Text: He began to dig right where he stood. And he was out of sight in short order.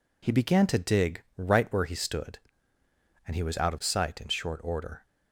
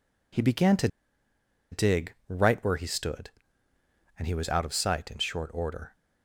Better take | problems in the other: first | pauses between "to" and "dig"; noticeable; at 0.8 s; 0.84 s long

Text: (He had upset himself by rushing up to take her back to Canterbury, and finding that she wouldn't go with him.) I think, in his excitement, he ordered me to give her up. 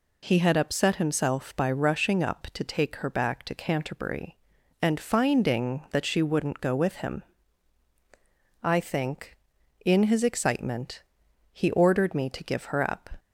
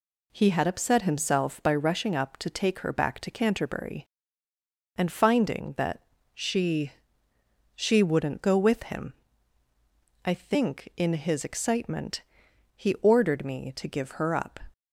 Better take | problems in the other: first | pauses between "that" and "she"; slight; at 6.0 s; 0.30 s long // says "she" twice; at 7.7 s

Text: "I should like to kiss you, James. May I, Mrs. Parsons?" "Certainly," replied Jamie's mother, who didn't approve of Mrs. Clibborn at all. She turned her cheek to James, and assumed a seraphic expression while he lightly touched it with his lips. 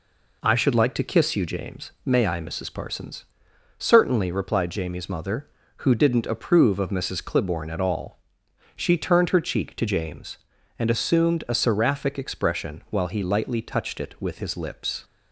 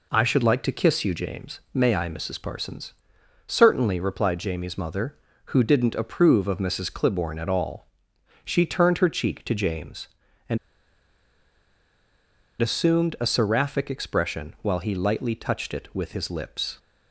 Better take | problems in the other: first | pauses between "and" and "assumed"; strong; at 10.5 s; 2.0 s long

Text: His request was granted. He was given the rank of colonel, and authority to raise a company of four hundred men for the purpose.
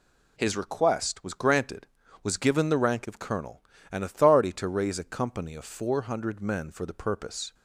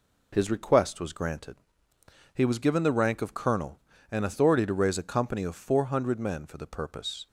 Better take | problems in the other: second | skips "He"; at 2.0 s

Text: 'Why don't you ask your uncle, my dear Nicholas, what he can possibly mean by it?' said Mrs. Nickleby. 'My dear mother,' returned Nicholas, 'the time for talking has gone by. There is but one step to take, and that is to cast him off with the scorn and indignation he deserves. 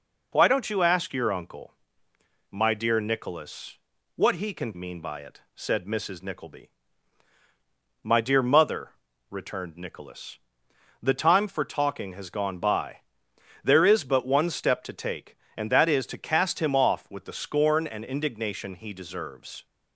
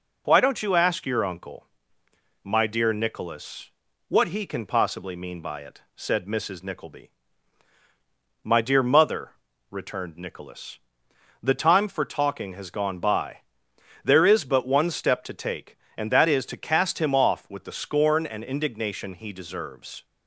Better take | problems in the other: second | skips "possibly"; at 4.7 s

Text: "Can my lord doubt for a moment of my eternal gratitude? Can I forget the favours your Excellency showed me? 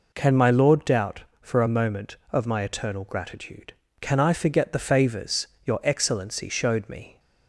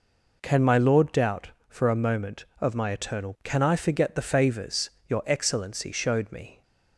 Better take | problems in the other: first | skips "gratitude"; at 3.3 s // pauses between "favours" and "your"; slight; at 4.8 s; 0.18 s long; slight in the first

